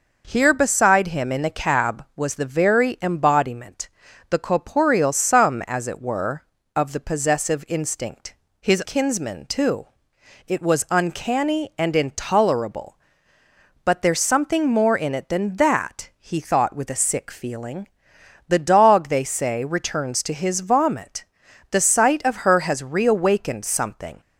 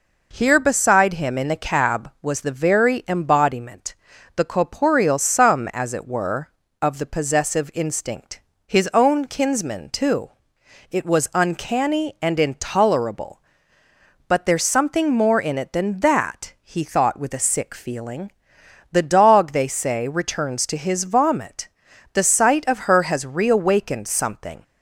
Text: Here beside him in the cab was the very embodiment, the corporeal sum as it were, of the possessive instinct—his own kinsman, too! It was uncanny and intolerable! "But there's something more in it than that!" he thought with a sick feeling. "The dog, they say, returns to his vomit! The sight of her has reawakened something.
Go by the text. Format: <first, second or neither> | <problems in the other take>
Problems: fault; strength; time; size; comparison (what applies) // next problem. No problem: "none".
second | skips "own"; at 8.8 s